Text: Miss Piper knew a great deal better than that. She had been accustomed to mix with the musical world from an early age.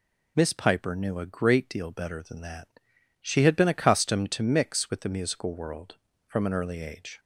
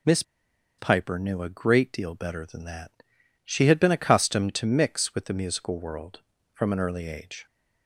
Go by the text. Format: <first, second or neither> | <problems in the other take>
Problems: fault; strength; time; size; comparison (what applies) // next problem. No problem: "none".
first | pauses between "Miss" and "Piper"; noticeable; at 0.2 s; 0.56 s long